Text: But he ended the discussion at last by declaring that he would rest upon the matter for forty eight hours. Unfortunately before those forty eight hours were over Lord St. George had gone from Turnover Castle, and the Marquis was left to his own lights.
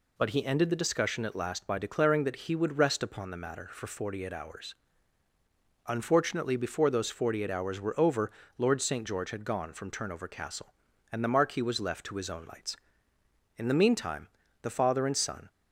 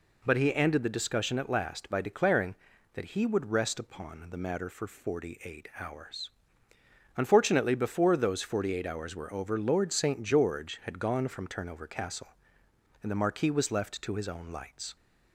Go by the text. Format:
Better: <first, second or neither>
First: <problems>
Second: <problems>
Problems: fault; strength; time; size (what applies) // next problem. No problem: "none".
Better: second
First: pauses between "over" and "Lord"; slight; at 8.3 s; 0.26 s long // goes on to say "In the meantime the father and son"; strong; from 13.5 s on; 1.9 s long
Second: none